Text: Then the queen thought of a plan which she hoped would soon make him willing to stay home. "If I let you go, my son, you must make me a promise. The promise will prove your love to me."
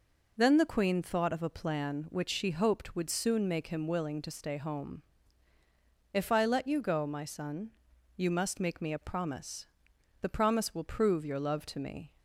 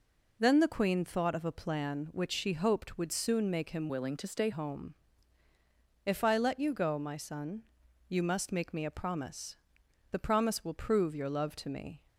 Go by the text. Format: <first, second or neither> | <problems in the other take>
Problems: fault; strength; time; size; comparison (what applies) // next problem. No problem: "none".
first | changes voice from "willing" to "stay"; from 3.8 to 4.4 s; 0.6 s long